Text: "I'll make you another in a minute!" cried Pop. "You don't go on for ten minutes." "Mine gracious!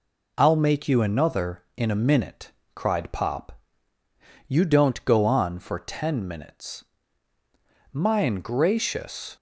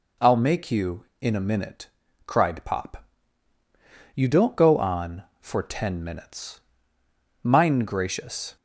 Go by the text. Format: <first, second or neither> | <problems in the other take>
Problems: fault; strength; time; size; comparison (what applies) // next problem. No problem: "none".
first | skips "another"; at 1.1 s